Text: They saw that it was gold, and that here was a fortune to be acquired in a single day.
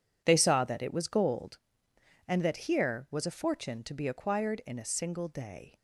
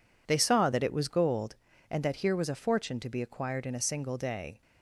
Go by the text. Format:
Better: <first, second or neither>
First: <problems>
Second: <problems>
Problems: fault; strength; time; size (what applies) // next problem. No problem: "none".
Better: neither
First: none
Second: none